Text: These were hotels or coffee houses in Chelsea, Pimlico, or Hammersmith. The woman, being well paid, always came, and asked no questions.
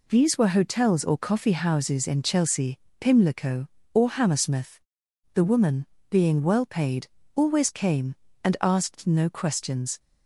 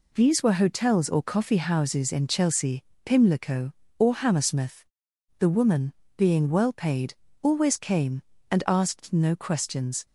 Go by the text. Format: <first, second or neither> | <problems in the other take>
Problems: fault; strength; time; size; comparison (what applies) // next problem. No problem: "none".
neither | none